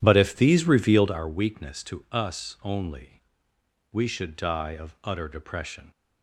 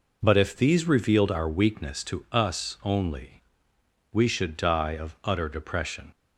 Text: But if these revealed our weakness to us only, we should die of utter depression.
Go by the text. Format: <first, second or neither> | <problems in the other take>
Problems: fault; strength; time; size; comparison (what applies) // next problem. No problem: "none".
second | starts louder than the rest; strong; until 1.1 s; 11 dB